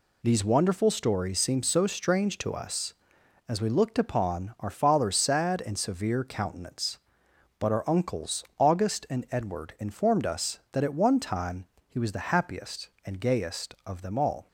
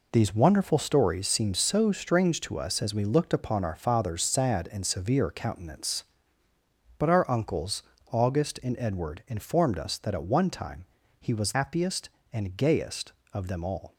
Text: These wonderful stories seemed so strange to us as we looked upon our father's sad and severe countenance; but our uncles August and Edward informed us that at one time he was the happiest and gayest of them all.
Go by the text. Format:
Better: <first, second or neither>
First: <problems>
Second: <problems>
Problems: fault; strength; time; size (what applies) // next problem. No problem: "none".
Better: first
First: pauses between "time" and "he"; slight; at 11.6 s; 0.20 s long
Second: pauses between "uncles" and "August"; slight; at 7.8 s; 0.26 s long // pauses between "time" and "he"; slight; at 10.8 s; 0.34 s long // skips "the"; at 11.5 s